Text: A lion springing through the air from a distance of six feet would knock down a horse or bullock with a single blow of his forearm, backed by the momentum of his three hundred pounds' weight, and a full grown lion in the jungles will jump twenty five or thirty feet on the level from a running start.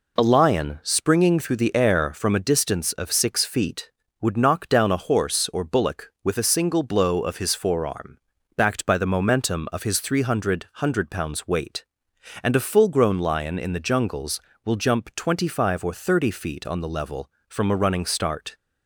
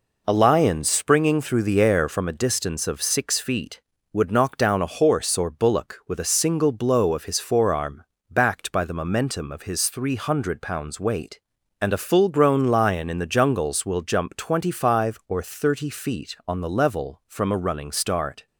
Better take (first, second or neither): second